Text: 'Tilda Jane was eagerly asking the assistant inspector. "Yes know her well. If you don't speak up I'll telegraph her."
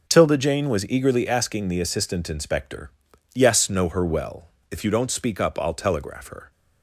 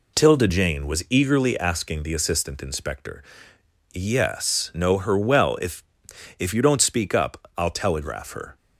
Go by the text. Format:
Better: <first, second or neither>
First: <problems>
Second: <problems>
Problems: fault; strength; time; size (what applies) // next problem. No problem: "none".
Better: first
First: none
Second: says "If" twice; at 6.3 s